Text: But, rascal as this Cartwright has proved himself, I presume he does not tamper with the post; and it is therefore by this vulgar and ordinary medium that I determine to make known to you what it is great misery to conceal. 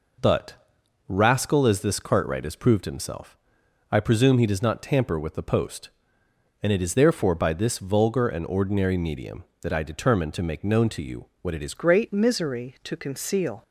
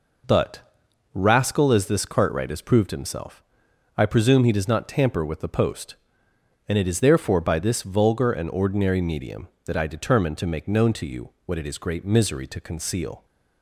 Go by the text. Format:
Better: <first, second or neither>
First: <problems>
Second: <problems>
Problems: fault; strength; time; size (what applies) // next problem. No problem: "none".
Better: second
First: changes voice at "great"; from 11.7 s on; 1.9 s long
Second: none